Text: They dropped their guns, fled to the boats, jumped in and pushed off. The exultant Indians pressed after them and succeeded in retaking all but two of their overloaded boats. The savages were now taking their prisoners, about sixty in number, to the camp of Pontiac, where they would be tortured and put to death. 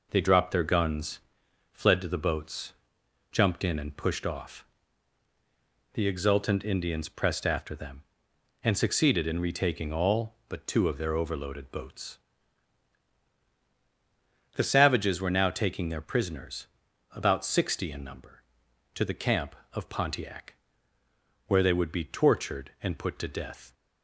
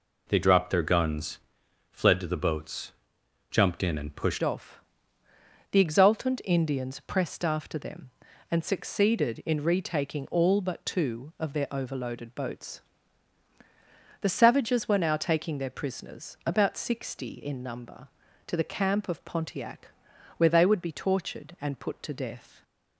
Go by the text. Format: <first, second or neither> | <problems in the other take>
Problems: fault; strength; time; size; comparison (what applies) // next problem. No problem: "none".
first | changes voice at "off"; from 4.4 s on; 18.2 s long // stays silent after the last word; slight; from 22.4 s on; 0.5 s long